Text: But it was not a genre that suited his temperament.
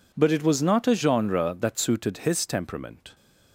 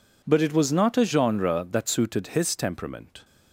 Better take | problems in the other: neither | none

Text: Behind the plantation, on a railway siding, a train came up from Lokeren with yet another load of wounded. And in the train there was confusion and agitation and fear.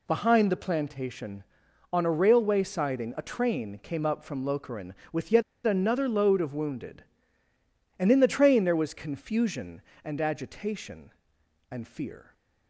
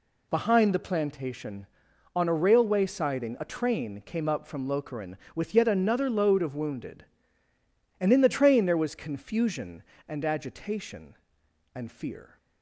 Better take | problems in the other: second | pauses between "yet" and "another"; slight; at 5.4 s; 0.24 s long

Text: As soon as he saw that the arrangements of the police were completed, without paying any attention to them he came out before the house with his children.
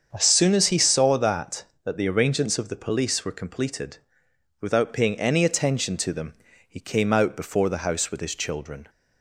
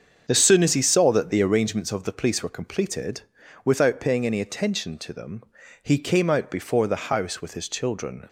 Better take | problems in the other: second | starts louder than the rest; strong; until 1.1 s; 7 dB; strong in the second // says "that" twice; at 1.8 s // pauses between "them" and "he"; slight; at 6.3 s; 0.34 s long; also in the second

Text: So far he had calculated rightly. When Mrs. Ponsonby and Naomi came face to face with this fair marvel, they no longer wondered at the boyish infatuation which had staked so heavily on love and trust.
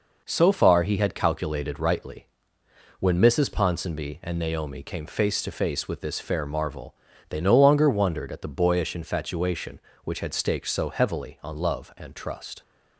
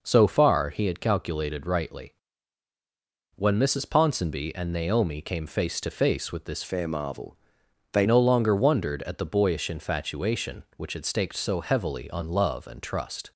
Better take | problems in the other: first | changes voice from "fair" to "they"; from 6.6 to 8.0 s; 1.4 s long

